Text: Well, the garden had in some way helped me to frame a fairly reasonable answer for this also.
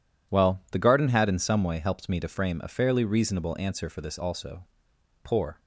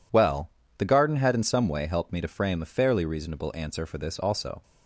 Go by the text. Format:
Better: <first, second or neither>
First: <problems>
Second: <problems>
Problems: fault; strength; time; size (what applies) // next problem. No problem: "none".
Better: second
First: goes on to say "Poor"; slight; from 5.2 s on; 0.36 s long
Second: none